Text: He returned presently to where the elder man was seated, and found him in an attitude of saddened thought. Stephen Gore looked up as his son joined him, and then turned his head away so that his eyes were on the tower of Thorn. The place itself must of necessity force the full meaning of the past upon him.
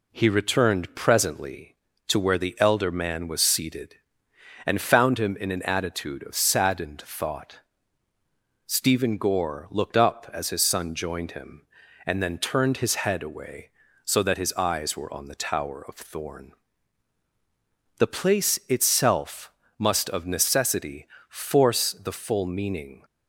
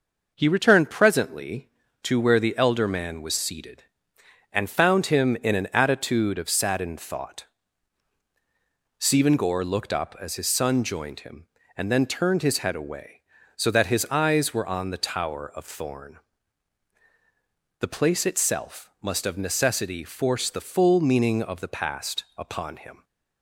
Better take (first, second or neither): second